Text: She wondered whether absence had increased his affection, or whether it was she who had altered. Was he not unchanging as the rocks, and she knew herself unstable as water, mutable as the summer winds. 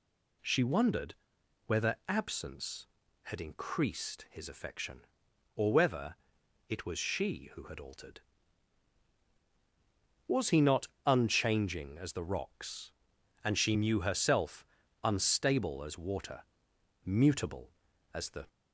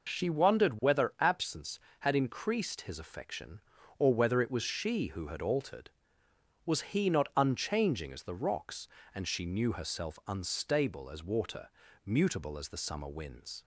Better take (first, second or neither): second